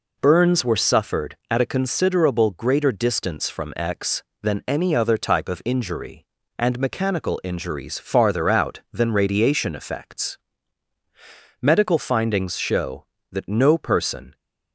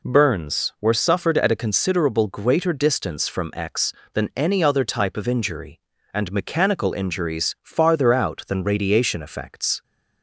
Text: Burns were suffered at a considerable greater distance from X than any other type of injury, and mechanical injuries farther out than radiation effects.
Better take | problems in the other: second | goes on to say "Medical findings show that no person"; strong; from 11.6 s on; 2.7 s long

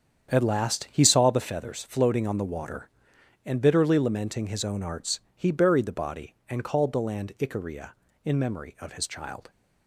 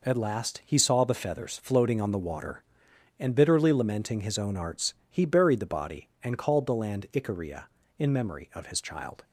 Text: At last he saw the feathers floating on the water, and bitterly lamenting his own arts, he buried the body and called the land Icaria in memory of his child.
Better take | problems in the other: second | starts louder than the rest; strong; until 1.5 s; 8.5 dB

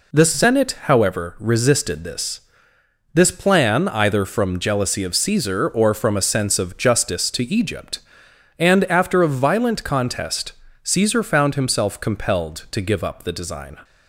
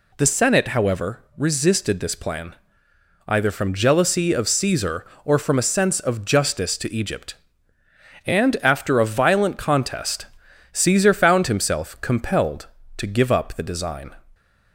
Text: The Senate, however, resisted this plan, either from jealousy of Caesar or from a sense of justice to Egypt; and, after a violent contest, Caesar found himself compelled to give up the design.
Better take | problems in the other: second | says "this" twice; at 3.1 s

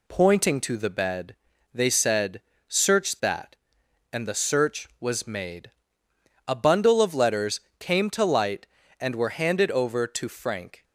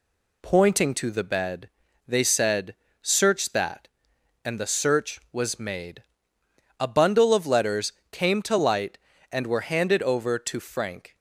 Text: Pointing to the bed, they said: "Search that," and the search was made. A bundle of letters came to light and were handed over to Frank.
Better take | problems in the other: neither | pauses between "letters" and "came"; slight; the same in both

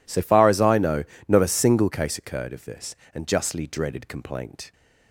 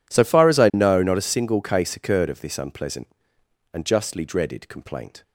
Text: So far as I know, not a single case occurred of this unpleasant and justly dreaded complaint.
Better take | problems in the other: second | skips "unpleasant"; at 3.0 s

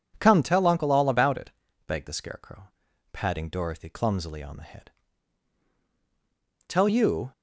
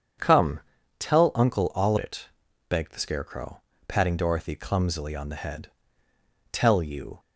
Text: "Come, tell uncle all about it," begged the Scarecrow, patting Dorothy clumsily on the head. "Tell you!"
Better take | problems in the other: first | skips "about"; at 1.9 s

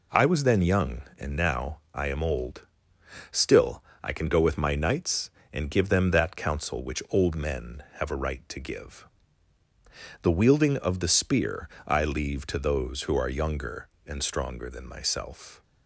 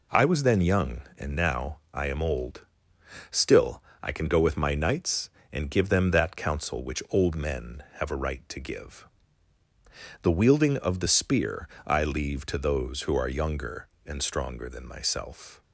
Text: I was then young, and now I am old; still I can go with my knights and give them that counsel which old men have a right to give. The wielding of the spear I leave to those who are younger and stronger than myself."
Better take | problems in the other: neither | pauses between "now" and "I"; slight; the same in both // pauses between "still" and "I"; slight; the same in both // pauses between "spear" and "I"; slight; the same in both

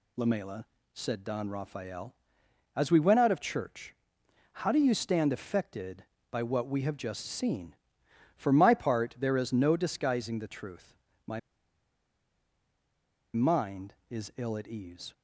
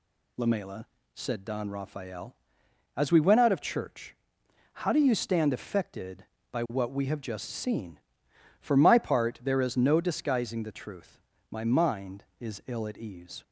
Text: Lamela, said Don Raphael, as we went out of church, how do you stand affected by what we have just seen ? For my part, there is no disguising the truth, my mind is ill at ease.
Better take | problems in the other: second | pauses between "my" and "mind"; strong; at 11.3 s; 1.9 s long

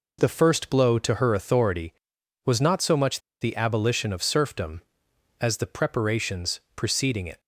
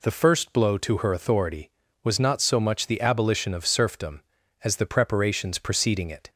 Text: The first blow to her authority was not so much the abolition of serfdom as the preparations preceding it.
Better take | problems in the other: second | pauses between "much" and "the"; slight; at 3.1 s; 0.21 s long // pauses between "preparations" and "preceding"; slight; at 6.5 s; 0.16 s long

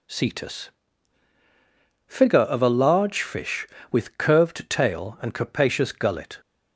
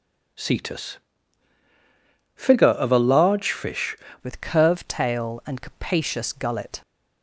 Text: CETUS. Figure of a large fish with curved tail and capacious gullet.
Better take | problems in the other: first | changes voice at "with"; from 4.2 s on; 2.6 s long

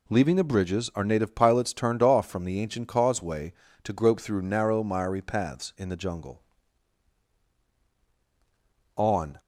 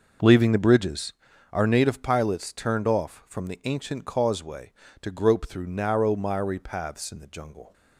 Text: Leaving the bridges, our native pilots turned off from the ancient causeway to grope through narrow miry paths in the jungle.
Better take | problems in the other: second | goes on to say "On"; slight; from 8.9 s on; 0.44 s long

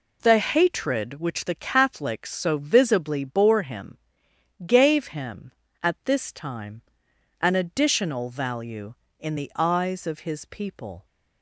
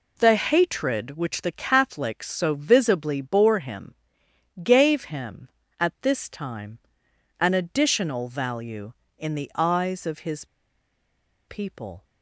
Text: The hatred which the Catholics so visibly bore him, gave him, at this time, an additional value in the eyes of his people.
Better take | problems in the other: first | pauses between "his" and "people"; at 10.4 s; 1.0 s long

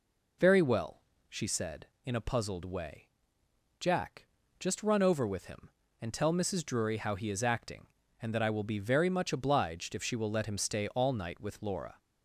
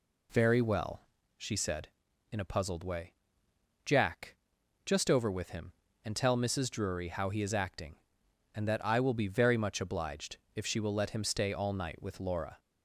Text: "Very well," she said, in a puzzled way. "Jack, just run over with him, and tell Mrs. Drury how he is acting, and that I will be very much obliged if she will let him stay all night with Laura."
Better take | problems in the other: first | skips "run"; at 5.1 s // pauses between "obliged" and "if"; slight; at 10.3 s; 0.18 s long

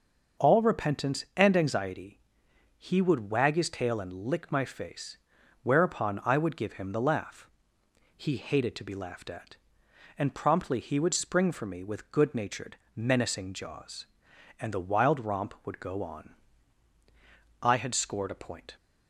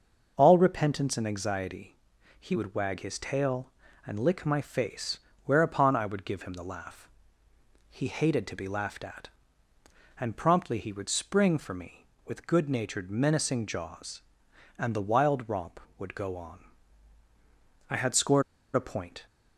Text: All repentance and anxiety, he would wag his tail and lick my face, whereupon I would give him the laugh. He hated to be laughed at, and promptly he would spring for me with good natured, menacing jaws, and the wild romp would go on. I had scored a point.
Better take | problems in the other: first | starts louder than the rest; until 1.3 s; 6.5 dB; also in the first // pauses between "scored" and "a"; slight; at 18.4 s; 0.33 s long

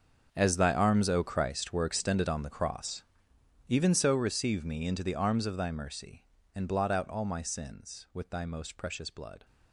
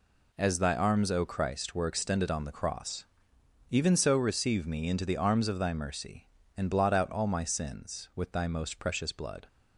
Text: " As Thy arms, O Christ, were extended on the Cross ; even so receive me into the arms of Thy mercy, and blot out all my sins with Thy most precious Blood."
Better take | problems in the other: second | gets quieter; strong; throughout; 15 dB

